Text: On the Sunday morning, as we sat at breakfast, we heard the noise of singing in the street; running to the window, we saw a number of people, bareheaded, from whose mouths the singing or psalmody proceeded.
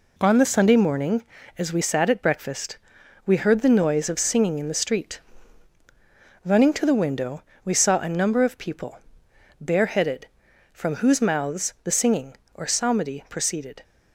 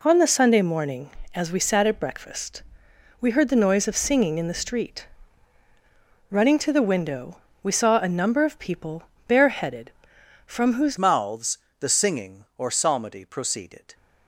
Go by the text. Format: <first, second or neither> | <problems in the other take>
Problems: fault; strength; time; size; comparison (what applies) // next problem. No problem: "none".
first | changes voice at "mouths"; from 10.9 s on; 3.0 s long // pauses between "mouths" and "the"; slight; at 11.5 s; 0.20 s long